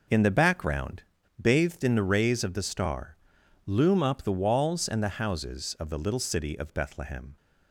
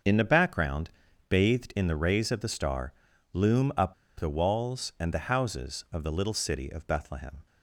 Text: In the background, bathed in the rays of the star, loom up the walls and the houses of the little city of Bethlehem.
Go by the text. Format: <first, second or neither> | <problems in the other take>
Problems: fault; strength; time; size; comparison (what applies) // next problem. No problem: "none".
first | starts louder than the rest; until 1.4 s; 6.5 dB // pauses between "up" and "the"; slight; at 3.9 s; 0.25 s long